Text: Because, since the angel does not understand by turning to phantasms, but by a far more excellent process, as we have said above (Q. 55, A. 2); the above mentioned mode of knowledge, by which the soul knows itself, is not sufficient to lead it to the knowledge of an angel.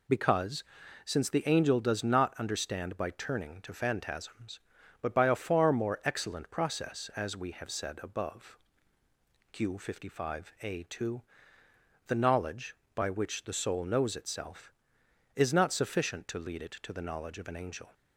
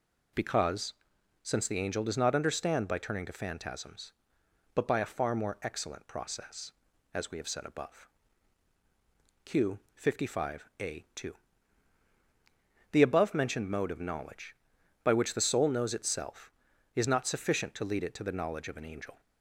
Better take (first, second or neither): second